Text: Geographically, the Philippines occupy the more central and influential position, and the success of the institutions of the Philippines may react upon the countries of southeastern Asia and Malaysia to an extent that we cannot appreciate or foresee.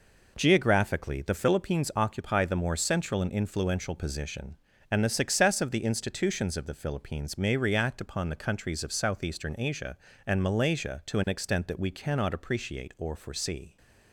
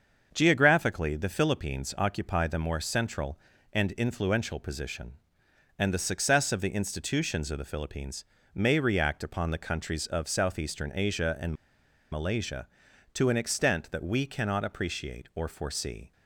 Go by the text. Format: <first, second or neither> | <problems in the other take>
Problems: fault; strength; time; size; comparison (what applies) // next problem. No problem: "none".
first | starts louder than the rest; until 1.3 s; 6.5 dB // pauses between "Philippines" and "may"; slight; at 8.2 s; 0.30 s long // pauses between "and" and "Malaysia"; noticeable; at 11.5 s; 0.57 s long